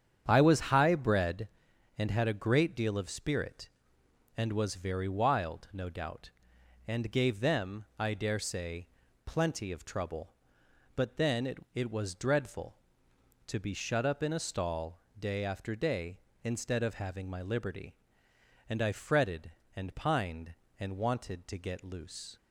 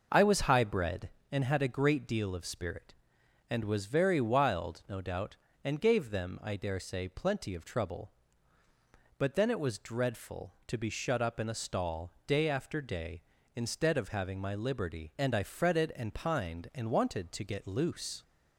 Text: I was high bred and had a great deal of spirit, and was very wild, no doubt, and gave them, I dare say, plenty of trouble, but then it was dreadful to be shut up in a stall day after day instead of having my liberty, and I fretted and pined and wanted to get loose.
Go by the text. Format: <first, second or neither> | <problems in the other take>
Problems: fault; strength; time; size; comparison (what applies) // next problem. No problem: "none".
second | starts louder than the rest; strong; until 1.2 s; 8.5 dB // says "it" twice; at 11.7 s // pauses between "stall" and "day"; slight; at 14.9 s; 0.18 s long; slight in the second